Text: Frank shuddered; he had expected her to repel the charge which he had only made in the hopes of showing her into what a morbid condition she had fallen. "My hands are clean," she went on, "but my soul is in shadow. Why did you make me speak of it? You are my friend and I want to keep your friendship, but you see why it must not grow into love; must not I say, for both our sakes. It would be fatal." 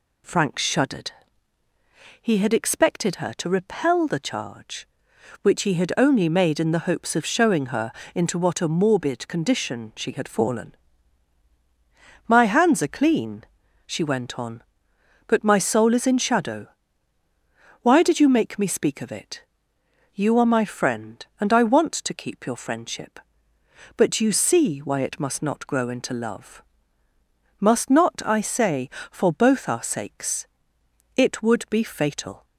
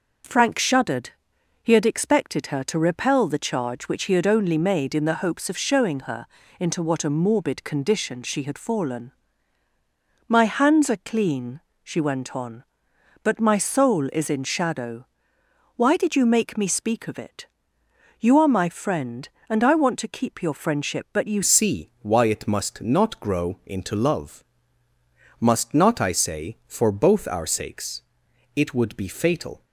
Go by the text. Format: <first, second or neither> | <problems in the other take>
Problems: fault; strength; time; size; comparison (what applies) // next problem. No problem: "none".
first | starts louder than the rest; until 1.7 s; 6.5 dB // pauses between "her" and "into"; slight; at 6.2 s; 0.34 s long; slight in the first // changes voice at "see"; from 21.4 s on; 8.2 s long